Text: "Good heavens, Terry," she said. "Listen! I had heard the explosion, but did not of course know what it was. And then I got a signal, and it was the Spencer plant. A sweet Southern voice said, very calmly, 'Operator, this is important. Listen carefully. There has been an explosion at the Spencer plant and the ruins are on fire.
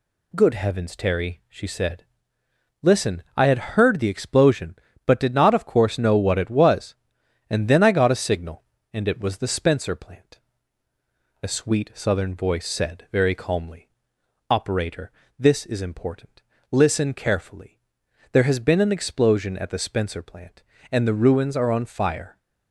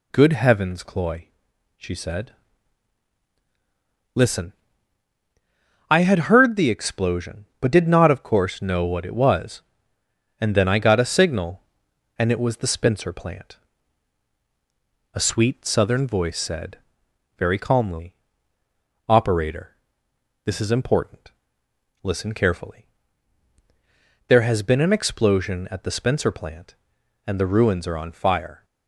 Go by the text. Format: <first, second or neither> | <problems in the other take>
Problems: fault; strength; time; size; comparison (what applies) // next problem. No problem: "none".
first | says "Cloy" for "Terry"; at 0.8 s